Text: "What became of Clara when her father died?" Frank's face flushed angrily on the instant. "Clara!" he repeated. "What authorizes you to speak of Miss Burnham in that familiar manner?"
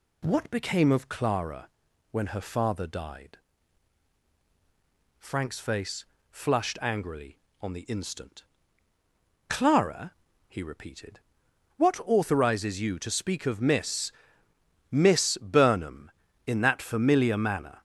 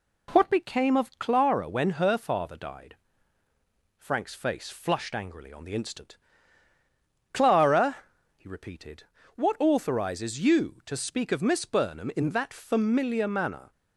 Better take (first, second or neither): second